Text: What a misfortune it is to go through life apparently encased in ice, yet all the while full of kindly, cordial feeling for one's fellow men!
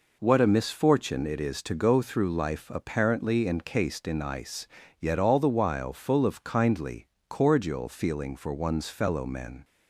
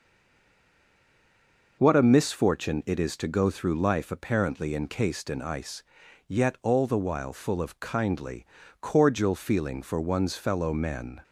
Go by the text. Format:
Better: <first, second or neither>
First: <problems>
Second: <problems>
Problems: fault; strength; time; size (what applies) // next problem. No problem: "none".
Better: first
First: none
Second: stays silent before the first word; noticeable; until 1.7 s; 1.7 s long